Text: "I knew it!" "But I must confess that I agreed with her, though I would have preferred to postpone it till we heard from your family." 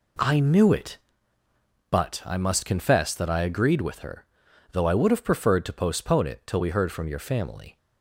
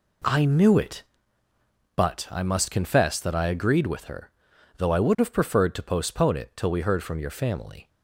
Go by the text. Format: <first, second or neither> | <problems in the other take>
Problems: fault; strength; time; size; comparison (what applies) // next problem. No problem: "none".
neither | none